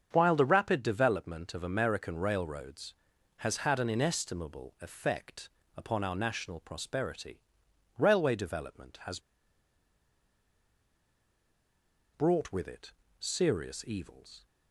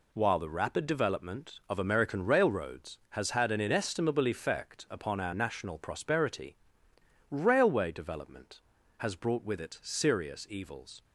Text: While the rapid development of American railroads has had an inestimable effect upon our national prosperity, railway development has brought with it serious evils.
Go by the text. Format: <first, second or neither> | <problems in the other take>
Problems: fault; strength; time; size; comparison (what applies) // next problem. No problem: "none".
second | starts louder than the rest; strong; until 1.1 s; 7 dB // pauses between "effect" and "upon"; slight; at 5.4 s; 0.30 s long // pauses between "has" and "brought"; strong; at 9.1 s; 2.9 s long // pauses between "it" and "serious"; slight; at 12.9 s; 0.26 s long